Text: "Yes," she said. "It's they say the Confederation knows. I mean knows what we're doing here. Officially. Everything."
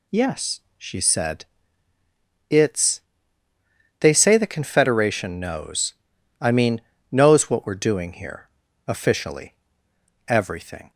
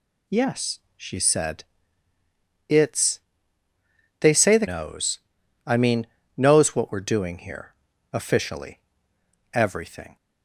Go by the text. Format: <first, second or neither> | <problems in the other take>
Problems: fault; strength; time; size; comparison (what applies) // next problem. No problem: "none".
first | pauses between "It's" and "they"; at 3.2 s; 1.0 s long; also in the first // skips "Confederation"; at 4.6 s // pauses between "mean" and "knows"; slight; at 6.0 s; 0.32 s long; slight in the first